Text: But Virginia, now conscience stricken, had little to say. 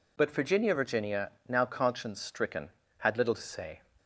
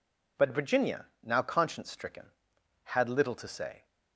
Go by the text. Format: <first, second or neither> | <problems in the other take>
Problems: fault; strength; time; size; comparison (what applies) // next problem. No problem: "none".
second | says "Virginia" twice; at 0.7 s